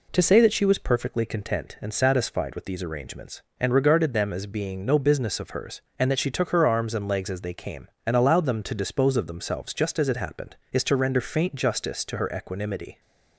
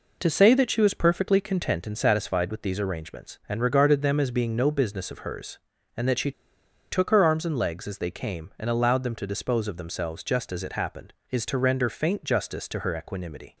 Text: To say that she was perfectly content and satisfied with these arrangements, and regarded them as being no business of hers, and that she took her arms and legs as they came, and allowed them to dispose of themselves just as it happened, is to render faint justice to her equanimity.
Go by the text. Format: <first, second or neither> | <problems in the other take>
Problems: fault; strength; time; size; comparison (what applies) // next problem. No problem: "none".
first | pauses between "she" and "took"; noticeable; at 6.3 s; 0.59 s long